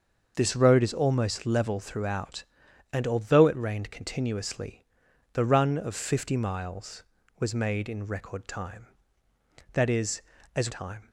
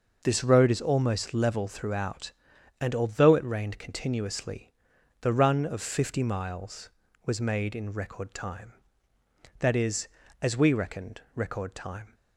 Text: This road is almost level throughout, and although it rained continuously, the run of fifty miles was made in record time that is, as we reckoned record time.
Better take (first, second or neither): second